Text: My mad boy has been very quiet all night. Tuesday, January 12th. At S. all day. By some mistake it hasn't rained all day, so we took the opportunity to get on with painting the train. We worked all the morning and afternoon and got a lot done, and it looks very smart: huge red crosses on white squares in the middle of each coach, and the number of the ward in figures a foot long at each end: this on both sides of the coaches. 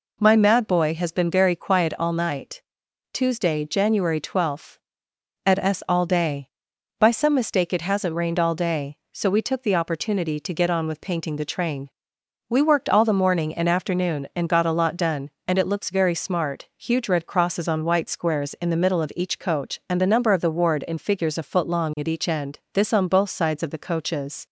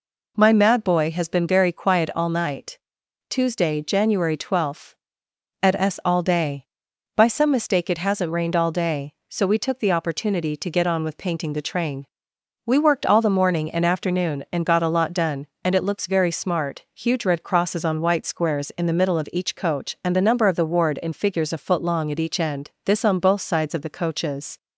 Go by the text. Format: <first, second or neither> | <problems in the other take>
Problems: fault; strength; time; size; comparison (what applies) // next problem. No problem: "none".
neither | none